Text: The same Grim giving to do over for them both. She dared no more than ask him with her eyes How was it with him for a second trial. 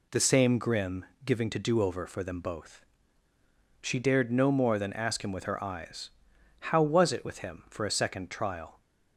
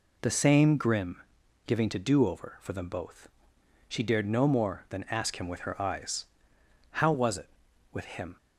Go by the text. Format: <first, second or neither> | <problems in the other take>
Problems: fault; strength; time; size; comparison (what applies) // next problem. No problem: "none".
first | pauses between "Grim" and "giving"; noticeable; at 1.2 s; 0.46 s long; slight in the first // pauses between "eyes" and "How"; noticeable; at 6.2 s; 0.66 s long; noticeable in the first // stops before "for a second trial"; at 8.3 s